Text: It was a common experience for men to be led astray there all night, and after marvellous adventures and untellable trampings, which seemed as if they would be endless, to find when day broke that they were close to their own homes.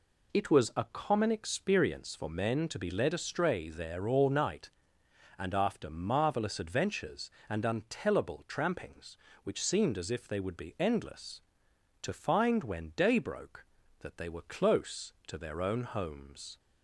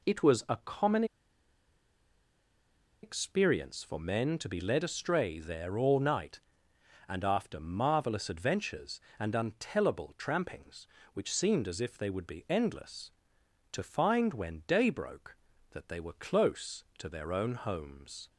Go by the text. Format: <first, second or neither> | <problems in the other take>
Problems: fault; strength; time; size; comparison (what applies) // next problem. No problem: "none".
first | pauses between "common" and "experience"; strong; at 1.0 s; 1.9 s long